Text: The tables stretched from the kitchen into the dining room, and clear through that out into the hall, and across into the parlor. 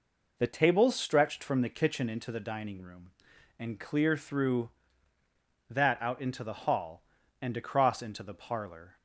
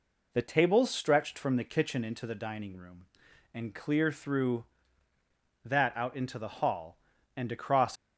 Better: first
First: none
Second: stops before "into the parlor"; at 7.9 s

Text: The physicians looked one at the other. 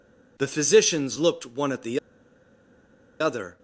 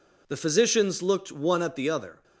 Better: second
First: pauses between "the" and "other"; at 1.9 s; 1.2 s long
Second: none

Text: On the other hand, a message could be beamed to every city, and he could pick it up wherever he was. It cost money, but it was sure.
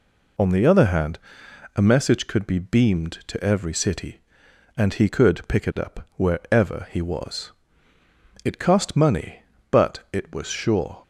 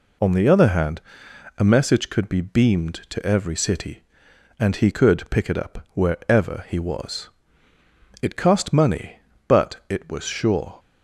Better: neither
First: none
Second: none

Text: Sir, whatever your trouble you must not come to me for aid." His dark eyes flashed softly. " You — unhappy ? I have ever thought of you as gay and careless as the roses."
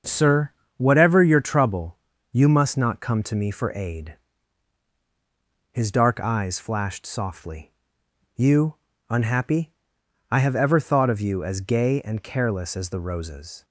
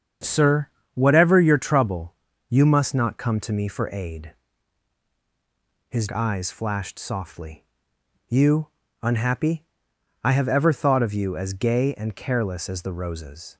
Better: first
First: starts louder than the rest; until 1.3 s; 7 dB // pauses between "trouble" and "you"; slight; at 1.9 s; 0.34 s long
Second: starts louder than the rest; strong; until 1.5 s; 8 dB // pauses between "trouble" and "you"; slight; at 2.1 s; 0.34 s long // skips "dark"; at 6.0 s

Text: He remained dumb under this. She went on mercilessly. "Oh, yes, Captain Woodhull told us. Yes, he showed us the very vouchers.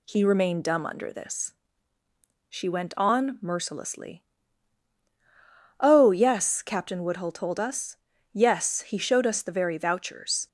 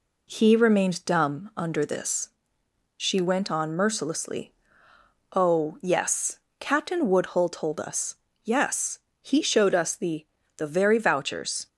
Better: first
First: none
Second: says "the" twice; at 10.5 s

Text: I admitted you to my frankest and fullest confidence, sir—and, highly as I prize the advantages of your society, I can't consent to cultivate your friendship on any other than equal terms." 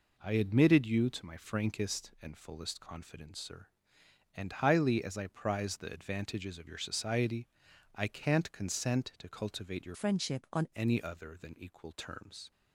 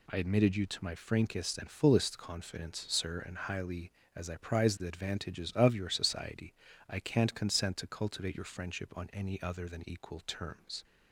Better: second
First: changes voice from "friendship" to "on"; from 9.9 to 10.6 s; 0.7 s long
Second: none

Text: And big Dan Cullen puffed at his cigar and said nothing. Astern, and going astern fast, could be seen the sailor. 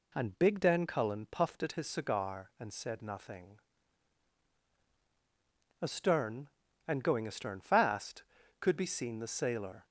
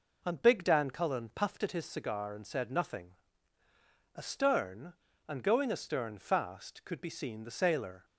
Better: neither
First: none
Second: none

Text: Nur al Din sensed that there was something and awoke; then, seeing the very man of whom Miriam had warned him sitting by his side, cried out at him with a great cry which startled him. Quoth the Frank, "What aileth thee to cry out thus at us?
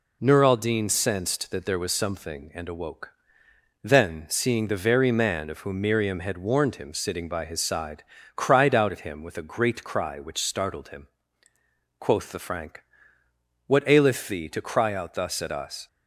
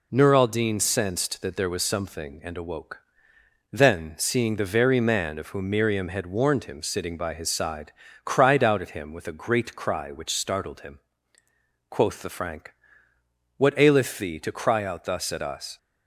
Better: neither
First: none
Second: none

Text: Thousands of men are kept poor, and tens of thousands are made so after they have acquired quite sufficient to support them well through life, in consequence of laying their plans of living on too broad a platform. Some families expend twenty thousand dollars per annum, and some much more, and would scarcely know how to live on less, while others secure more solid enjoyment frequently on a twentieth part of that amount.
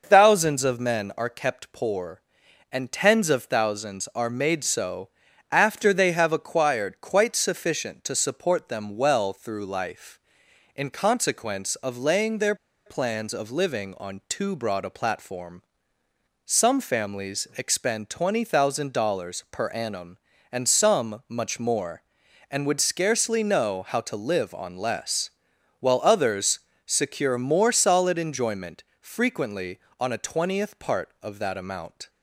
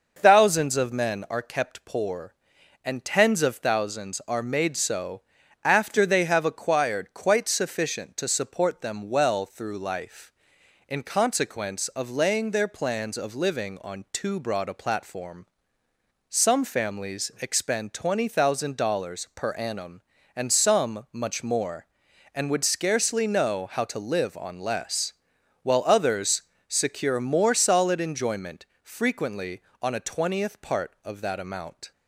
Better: second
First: pauses between "so" and "after"; at 5.0 s; 0.42 s long // pauses between "their" and "plans"; slight; at 12.5 s; 0.31 s long // pauses between "others" and "secure"; slight; at 26.5 s; 0.30 s long // pauses between "enjoyment" and "frequently"; slight; at 28.8 s; 0.16 s long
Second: pauses between "so" and "after"; at 5.2 s; 0.42 s long // pauses between "others" and "secure"; slight; at 26.4 s; 0.29 s long // pauses between "enjoyment" and "frequently"; slight; at 28.6 s; 0.16 s long

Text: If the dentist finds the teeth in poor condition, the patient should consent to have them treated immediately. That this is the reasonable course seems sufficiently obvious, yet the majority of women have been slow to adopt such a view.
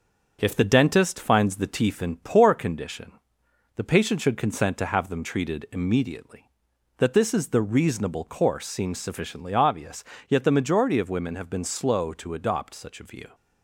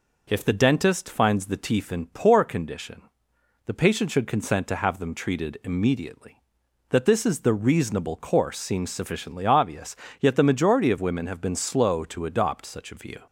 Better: second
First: gets quieter; throughout; 3.5 dB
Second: none

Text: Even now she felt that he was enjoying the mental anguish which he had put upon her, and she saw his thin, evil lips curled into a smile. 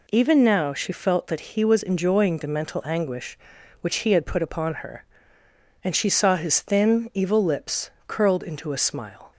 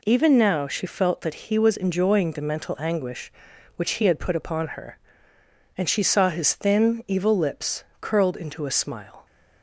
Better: neither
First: pauses between "lips" and "curled"; slight; at 7.8 s; 0.16 s long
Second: pauses between "lips" and "curled"; slight; at 7.8 s; 0.16 s long

